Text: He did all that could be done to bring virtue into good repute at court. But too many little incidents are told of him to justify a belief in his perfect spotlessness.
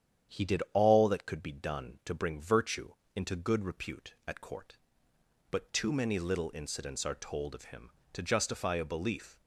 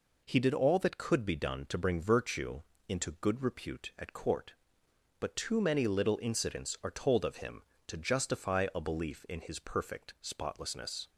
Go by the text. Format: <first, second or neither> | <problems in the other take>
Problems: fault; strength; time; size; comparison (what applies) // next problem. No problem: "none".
second | starts louder than the rest; strong; until 1.4 s; 9 dB // pauses between "virtue" and "into"; slight; at 2.9 s; 0.22 s long; slight in the second // stops before "in his perfect spotlessness"; at 9.3 s